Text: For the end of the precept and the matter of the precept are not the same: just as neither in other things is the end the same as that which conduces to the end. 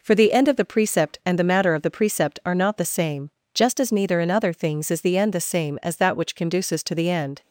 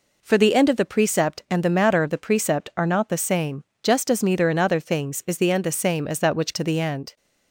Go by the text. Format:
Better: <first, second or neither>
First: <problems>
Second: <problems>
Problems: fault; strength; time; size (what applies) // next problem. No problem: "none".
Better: first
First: none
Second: skips "conduces"; at 6.5 s